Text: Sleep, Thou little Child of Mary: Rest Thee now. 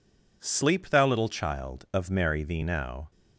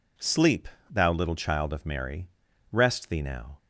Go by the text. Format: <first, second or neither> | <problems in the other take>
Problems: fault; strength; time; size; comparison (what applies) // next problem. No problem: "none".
second | skips "Rest"; at 2.4 s